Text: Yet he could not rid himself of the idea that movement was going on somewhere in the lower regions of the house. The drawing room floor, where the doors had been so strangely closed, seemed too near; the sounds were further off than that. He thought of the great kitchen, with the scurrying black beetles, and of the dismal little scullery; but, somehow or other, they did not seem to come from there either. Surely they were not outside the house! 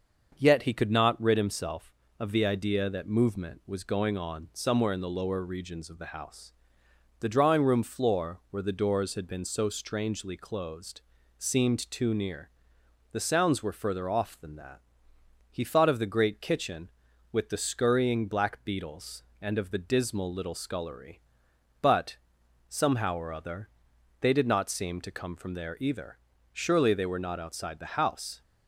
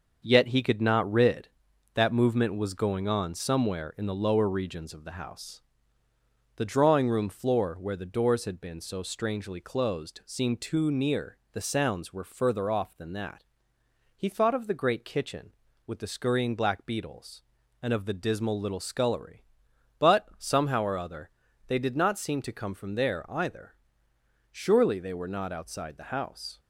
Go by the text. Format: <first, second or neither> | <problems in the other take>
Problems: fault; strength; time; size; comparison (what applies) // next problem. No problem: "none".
first | starts louder than the rest; until 1.2 s; 6.5 dB; also in the first // skips "himself of the idea"; at 1.7 s